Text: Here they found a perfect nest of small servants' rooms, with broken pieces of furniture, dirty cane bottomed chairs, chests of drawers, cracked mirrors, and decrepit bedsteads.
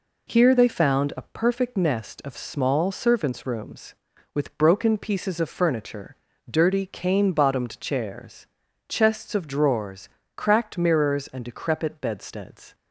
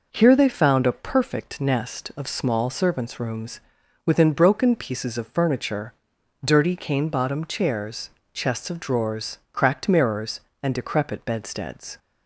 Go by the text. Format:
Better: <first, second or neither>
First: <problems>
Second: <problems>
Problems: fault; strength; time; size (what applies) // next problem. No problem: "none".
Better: first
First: none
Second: says "within" for "with"; at 4.0 s